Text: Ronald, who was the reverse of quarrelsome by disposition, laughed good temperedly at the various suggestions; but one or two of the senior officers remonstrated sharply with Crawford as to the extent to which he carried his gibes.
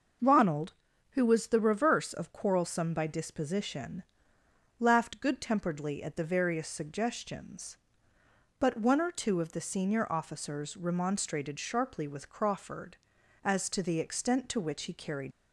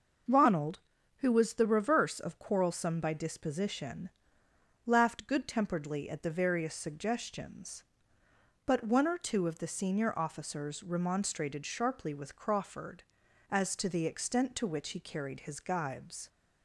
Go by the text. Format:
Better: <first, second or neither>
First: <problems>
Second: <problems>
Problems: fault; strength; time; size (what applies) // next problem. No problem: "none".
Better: second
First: starts louder than the rest; noticeable; until 1.6 s; 6 dB // stops before "his gibes"; at 15.3 s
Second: starts louder than the rest; until 1.6 s; 6 dB